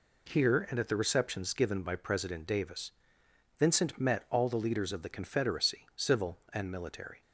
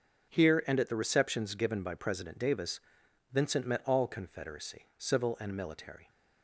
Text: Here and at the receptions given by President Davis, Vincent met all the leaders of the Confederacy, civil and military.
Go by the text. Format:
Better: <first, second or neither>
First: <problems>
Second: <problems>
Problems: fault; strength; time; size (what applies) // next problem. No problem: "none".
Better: first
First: none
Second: starts louder than the rest; until 1.3 s; 6.5 dB // skips "the leaders of the"; at 4.0 s